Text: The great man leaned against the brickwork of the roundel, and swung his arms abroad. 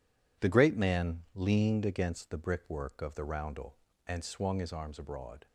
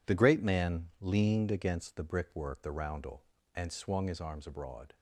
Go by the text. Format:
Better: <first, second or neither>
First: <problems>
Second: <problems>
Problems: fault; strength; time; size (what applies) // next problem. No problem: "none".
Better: first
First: none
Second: skips "of"; at 2.6 s